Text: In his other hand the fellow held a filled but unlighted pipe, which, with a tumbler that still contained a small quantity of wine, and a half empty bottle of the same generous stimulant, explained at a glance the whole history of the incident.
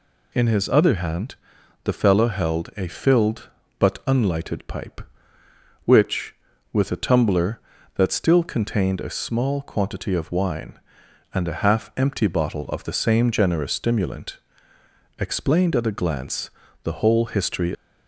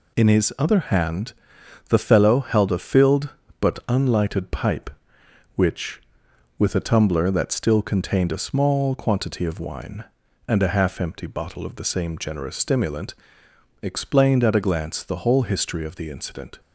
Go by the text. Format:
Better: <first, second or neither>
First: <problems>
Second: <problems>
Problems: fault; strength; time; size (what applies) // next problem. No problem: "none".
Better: second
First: pauses between "hand" and "the"; noticeable; at 1.3 s; 0.50 s long // pauses between "glance" and "the"; slight; at 16.4 s; 0.36 s long // stops before "of the incident"; at 17.7 s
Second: pauses between "hand" and "the"; noticeable; at 1.3 s; 0.54 s long